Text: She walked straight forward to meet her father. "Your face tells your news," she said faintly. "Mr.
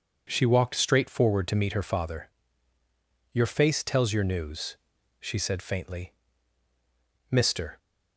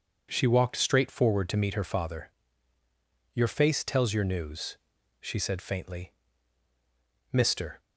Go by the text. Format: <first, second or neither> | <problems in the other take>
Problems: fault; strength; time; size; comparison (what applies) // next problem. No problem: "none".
neither | none